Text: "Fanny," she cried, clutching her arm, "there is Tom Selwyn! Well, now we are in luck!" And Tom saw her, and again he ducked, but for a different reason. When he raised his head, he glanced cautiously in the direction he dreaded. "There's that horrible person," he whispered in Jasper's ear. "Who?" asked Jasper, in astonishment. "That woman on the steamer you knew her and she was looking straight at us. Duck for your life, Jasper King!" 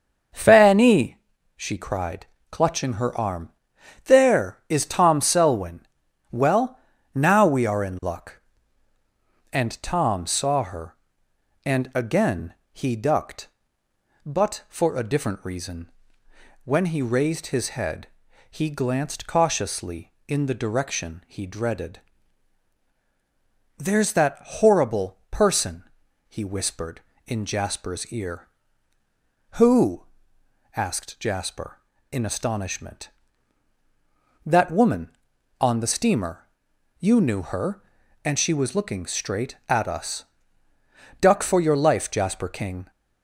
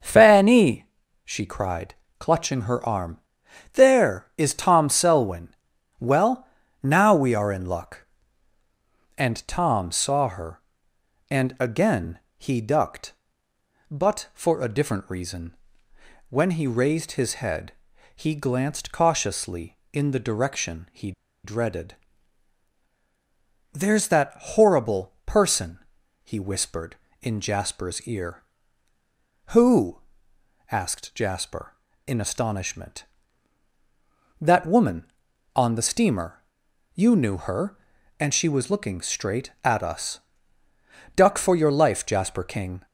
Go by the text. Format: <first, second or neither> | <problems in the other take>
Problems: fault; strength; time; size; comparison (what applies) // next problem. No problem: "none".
first | starts louder than the rest; noticeable; until 1.3 s; 6 dB; noticeable in the first // pauses between "again" and "he"; slight; at 12.1 s; 0.20 s long; slight in the first // pauses between "he" and "dreaded"; slight; at 21.1 s; 0.32 s long // pauses between "steamer" and "you"; noticeable; at 36.4 s; 0.52 s long; noticeable in the first